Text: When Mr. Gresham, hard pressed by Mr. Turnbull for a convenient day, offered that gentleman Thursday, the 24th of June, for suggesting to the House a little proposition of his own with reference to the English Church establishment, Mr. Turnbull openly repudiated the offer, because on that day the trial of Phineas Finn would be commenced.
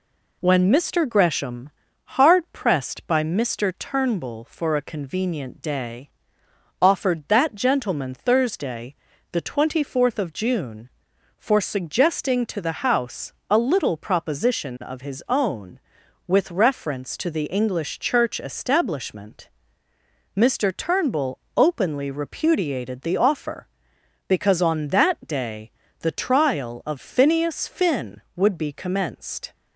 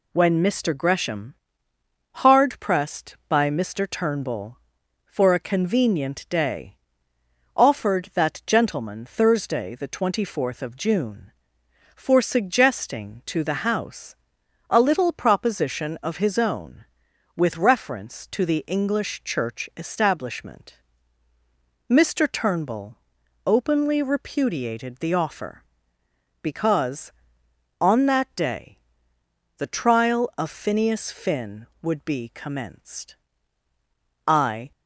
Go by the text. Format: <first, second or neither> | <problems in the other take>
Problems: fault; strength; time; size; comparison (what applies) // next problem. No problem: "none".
first | pauses between "House" and "a"; noticeable; at 14.1 s; 0.54 s long; slight in the first // pauses between "Turnbull" and "openly"; noticeable; at 22.9 s; 0.48 s long; slight in the first // pauses between "day" and "the"; noticeable; at 28.7 s; 0.80 s long; slight in the first // goes on to say "I"; slight; from 34.2 s on; 0.44 s long